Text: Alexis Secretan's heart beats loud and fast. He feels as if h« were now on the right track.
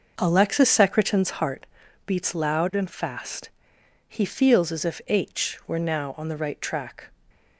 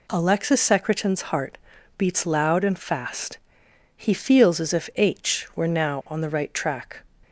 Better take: second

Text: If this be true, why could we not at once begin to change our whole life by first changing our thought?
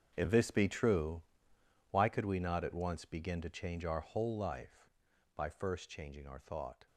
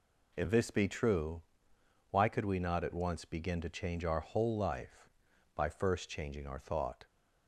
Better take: second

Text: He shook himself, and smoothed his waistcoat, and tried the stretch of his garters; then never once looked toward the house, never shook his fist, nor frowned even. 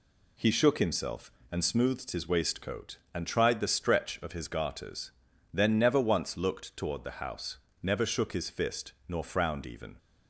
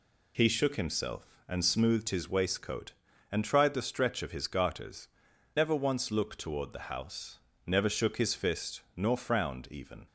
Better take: first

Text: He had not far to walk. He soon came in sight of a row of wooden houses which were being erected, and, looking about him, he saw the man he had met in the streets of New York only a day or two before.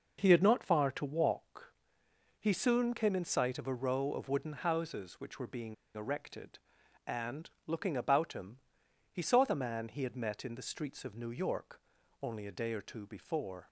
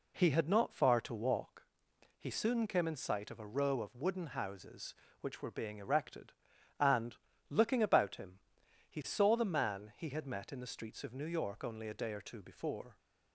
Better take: second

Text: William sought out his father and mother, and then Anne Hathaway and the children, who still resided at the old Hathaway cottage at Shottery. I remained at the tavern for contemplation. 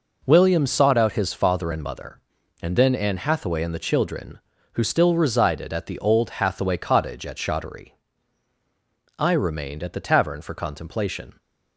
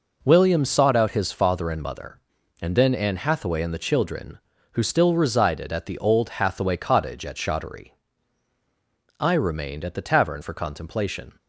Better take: neither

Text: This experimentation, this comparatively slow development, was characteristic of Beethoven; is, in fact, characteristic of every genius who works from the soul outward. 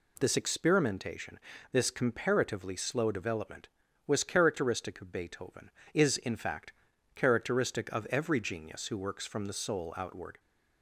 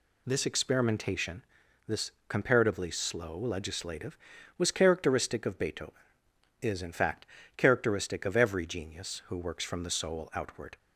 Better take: first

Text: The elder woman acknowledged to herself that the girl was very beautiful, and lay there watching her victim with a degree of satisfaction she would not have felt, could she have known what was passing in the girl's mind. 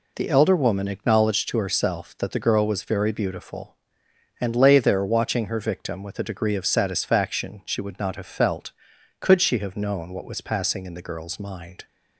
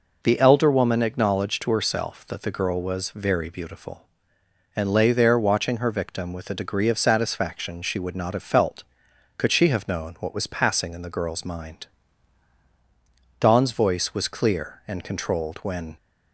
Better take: first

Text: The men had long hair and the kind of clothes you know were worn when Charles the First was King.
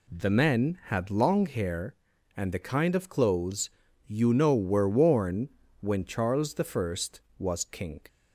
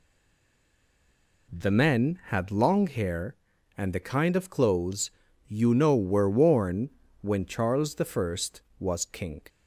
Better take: first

